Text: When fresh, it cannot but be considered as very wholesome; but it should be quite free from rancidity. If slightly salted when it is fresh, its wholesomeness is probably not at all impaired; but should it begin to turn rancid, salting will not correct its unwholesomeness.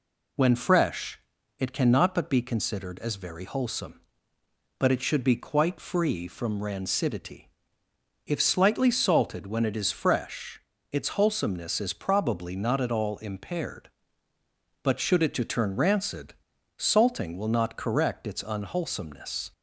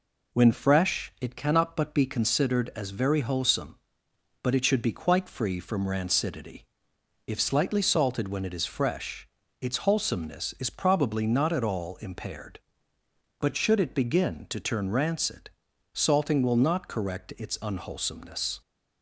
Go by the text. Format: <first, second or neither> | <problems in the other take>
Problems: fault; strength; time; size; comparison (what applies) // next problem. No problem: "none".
second | skips "begin"; at 15.3 s